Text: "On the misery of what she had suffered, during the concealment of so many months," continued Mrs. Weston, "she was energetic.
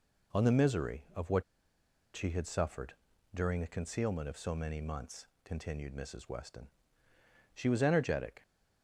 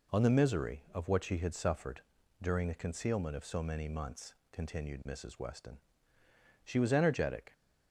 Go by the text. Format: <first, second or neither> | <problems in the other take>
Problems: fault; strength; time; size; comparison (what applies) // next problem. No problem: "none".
second | pauses between "what" and "she"; noticeable; at 1.4 s; 0.71 s long